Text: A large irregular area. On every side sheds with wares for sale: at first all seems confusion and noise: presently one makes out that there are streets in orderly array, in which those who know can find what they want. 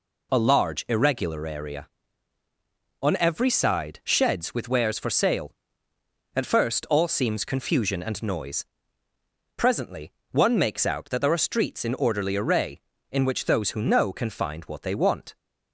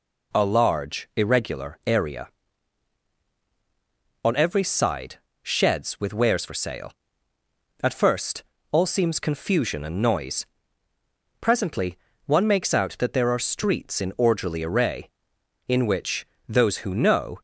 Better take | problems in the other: first | pauses between "side" and "sheds"; slight; at 5.1 s; 0.26 s long // pauses between "first" and "all"; slight; at 8.4 s; 0.28 s long // pauses between "presently" and "one"; slight; at 11.9 s; 0.30 s long; slight in the first // pauses between "which" and "those"; slight; at 16.2 s; 0.20 s long // stops before "can find what they want"; at 17.3 s

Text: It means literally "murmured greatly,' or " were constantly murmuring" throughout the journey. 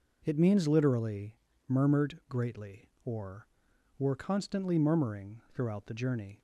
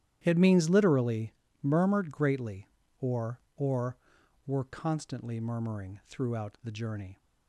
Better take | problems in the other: first | starts louder than the rest; strong; until 1.2 s; 11.5 dB // pauses between "literally" and "murmured"; slight; at 1.3 s; 0.30 s long; slight in the first // says "or" twice; at 3.5 s

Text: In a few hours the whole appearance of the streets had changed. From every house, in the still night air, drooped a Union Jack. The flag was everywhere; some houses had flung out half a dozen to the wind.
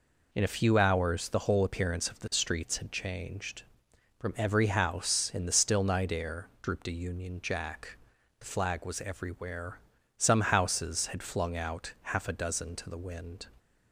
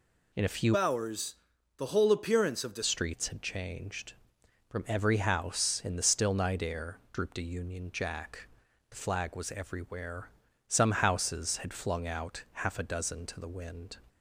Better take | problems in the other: first | changes voice from "hours" to "the"; from 0.7 to 2.8 s; 2.1 s long // pauses between "hours" and "the"; at 1.3 s; 0.40 s long // pauses between "out" and "half"; slight; at 12.4 s; 0.18 s long; slight in the first

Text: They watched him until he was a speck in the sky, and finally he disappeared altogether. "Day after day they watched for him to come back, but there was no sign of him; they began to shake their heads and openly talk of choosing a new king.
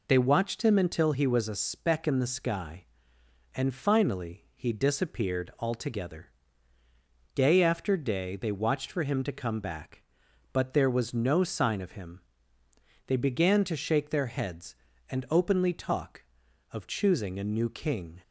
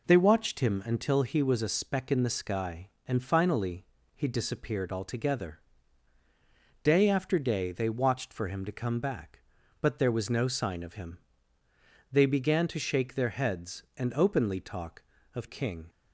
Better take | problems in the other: first | pauses between "finally" and "he"; slight; at 3.8 s; 0.28 s long // skips "choosing a new"; at 15.4 s

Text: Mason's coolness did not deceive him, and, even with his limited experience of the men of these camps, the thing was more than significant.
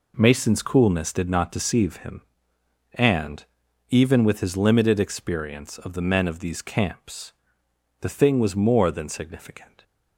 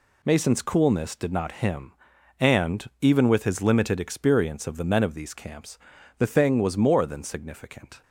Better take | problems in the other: first | skips "deceive"; at 1.5 s

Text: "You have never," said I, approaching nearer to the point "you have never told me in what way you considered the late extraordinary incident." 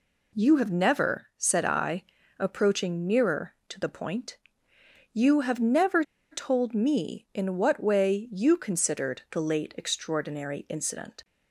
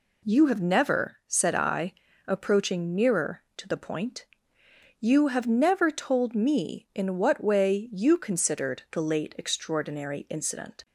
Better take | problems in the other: second | pauses between "point" and "you"; noticeable; at 4.3 s; 0.74 s long; noticeable in the second // pauses between "never" and "told"; slight; at 6.0 s; 0.29 s long

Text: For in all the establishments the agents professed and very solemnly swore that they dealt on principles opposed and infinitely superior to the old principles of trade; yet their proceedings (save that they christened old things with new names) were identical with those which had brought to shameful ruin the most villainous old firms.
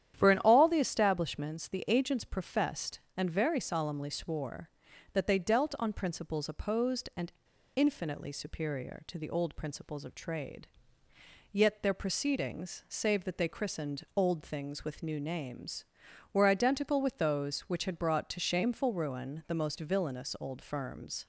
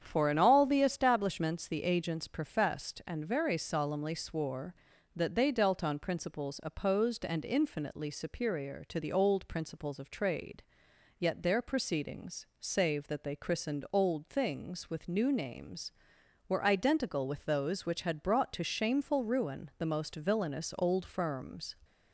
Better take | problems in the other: second | starts louder than the rest; strong; until 1.1 s; 10 dB; strong in the second // pauses between "and" and "infinitely"; at 7.3 s; 0.44 s long

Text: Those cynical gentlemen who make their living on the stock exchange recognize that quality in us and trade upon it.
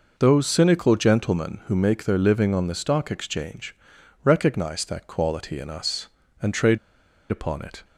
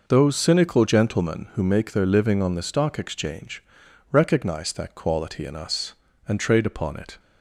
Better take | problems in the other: second | pauses between "exchange" and "recognize"; noticeable; at 3.7 s; 0.48 s long; noticeable in the second // pauses between "trade" and "upon"; noticeable; at 6.7 s; 0.51 s long

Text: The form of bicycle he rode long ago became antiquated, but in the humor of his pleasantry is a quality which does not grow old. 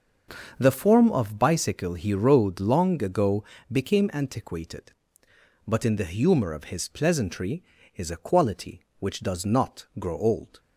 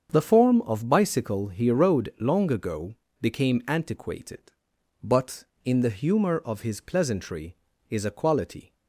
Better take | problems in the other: first | starts louder than the rest; strong; until 1.1 s; 7 dB; also in the first // pauses between "ago" and "became"; slight; at 2.9 s; 0.26 s long; slight in the first // stops before "which does not grow old"; at 8.7 s

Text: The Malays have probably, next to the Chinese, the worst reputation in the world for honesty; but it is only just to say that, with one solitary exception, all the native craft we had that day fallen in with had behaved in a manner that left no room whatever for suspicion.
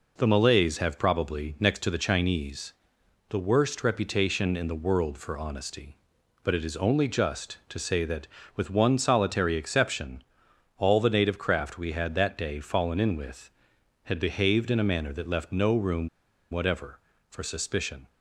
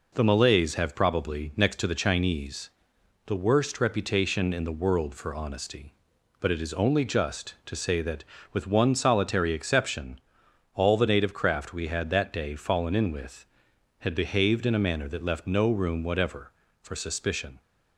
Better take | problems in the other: second | pauses between "room" and "whatever"; at 16.0 s; 0.42 s long

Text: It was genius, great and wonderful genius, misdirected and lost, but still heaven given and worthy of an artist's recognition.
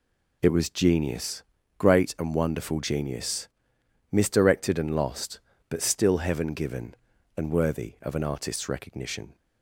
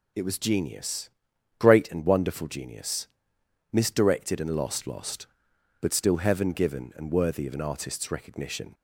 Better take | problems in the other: first | says "lost" twice; at 4.8 s

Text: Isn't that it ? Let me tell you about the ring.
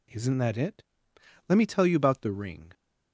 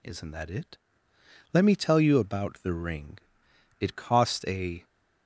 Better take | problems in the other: first | goes on to say "It cost a"; noticeable; from 3.7 s on; 1.0 s long

